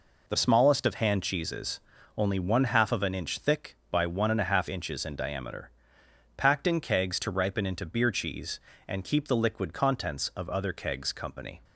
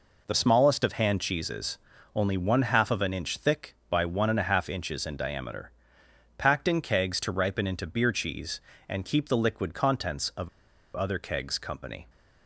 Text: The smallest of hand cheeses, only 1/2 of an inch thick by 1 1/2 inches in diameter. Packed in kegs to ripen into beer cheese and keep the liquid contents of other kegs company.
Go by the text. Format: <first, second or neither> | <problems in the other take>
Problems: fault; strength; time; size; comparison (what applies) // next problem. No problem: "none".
first | pauses between "of" and "other"; at 10.4 s; 0.45 s long